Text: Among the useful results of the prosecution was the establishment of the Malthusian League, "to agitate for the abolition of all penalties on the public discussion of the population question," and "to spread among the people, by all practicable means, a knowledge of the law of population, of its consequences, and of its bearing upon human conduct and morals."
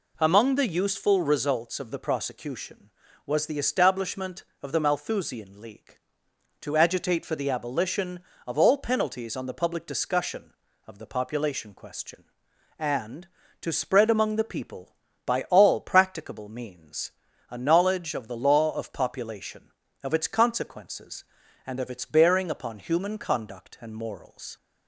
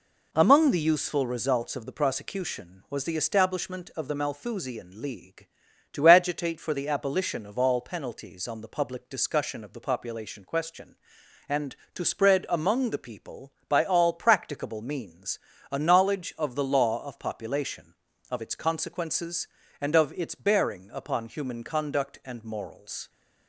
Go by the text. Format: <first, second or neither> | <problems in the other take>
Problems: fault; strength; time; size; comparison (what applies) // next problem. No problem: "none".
neither | none